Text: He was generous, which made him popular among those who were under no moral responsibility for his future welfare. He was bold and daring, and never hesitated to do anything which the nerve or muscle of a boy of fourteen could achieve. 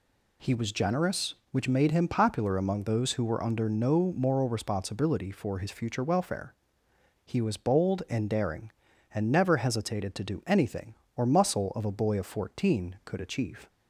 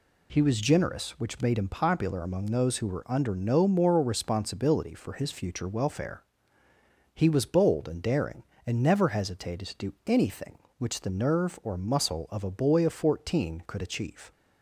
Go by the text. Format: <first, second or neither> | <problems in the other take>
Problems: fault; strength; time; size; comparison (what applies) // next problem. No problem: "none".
second | skips "which the nerve"; at 11.0 s